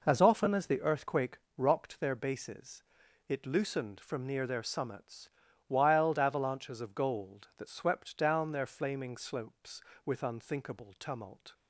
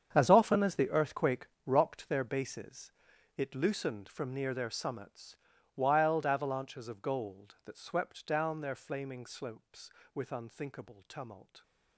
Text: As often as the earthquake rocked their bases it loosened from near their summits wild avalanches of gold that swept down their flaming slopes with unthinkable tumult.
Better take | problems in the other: first | gets quieter; strong; throughout; 14.5 dB // pauses between "earthquake" and "rocked"; slight; at 1.4 s; 0.18 s long; slight in the first // pauses between "bases" and "it"; noticeable; at 2.9 s; 0.46 s long; noticeable in the first // pauses between "summits" and "wild"; at 5.3 s; 0.40 s long; also in the first

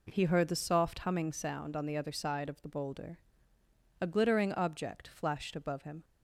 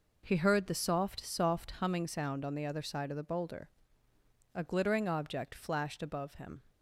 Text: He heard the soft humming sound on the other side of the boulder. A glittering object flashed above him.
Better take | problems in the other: first | says "soft" twice; at 1.2 s

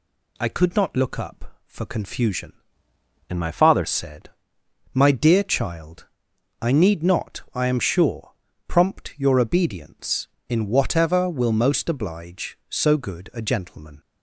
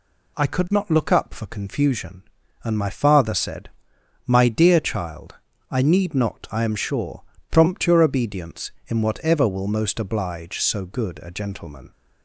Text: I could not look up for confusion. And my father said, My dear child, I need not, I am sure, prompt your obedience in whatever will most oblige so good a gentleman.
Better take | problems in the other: second | changes voice from "And" to "father"; from 3.2 to 3.8 s; 0.6 s long

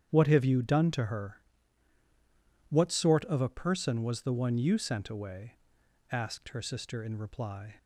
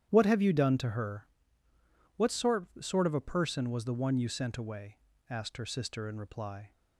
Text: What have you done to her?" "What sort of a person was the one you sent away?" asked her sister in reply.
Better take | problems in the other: first | starts louder than the rest; strong; until 1.1 s; 10.5 dB; strong in the first // says "sort" twice; at 2.8 s

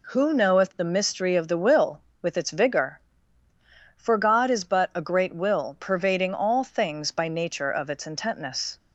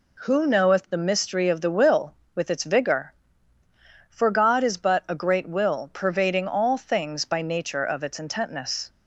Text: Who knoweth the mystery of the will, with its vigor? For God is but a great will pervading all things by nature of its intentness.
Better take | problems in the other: neither | none

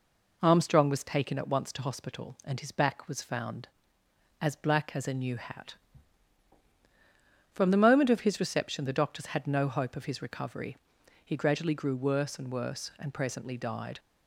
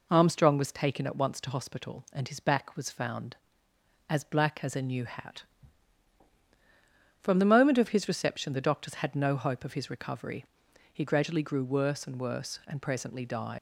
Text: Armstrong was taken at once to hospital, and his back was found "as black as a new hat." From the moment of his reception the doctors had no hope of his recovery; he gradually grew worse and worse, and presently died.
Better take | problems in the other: first | leaves "died" unfinished; at 13.5 s; 85 ms

